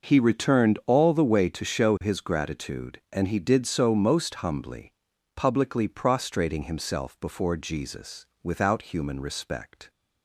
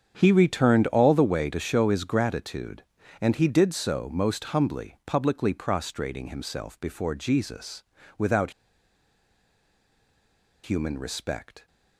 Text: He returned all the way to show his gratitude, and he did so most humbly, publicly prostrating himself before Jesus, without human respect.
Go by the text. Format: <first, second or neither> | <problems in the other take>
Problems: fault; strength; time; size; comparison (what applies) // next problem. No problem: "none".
first | starts louder than the rest; strong; until 1.1 s; 7.5 dB // pauses between "without" and "human"; strong; at 8.5 s; 2.1 s long